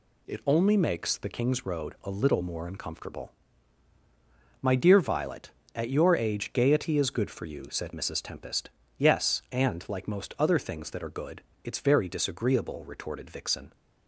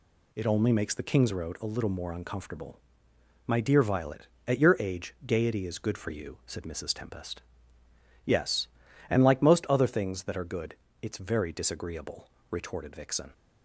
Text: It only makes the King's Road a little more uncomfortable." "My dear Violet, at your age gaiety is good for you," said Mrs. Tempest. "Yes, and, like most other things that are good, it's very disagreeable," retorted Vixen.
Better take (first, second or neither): neither